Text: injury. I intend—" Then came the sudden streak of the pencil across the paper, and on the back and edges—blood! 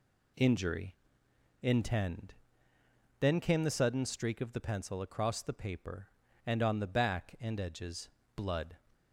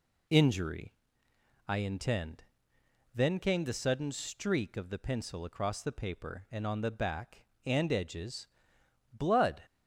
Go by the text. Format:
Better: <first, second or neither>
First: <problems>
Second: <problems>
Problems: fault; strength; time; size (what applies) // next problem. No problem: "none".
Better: second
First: skips "I"; at 1.2 s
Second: none